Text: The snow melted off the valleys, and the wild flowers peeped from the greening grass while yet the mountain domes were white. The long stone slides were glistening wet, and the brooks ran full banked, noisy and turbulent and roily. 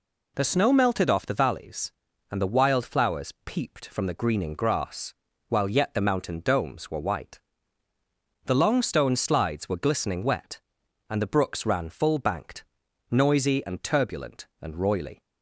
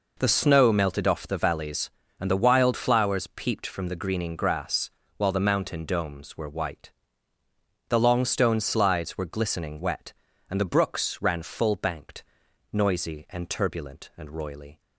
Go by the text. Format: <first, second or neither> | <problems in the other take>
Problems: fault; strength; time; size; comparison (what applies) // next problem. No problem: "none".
first | pauses between "grass" and "while"; slight; at 4.9 s; 0.26 s long; slight in the first // skips "yet"; at 5.3 s